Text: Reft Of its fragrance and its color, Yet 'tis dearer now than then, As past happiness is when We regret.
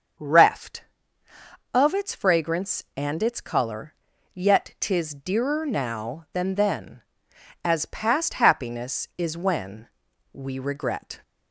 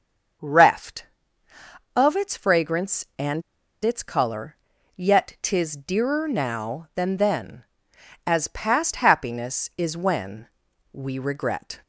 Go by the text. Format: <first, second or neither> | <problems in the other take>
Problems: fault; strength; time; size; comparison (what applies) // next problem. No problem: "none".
first | starts louder than the rest; until 2.3 s; 6.5 dB; also in the first // pauses between "and" and "its"; at 3.4 s; 0.41 s long // pauses between "when" and "We"; noticeable; at 10.4 s; 0.46 s long; noticeable in the first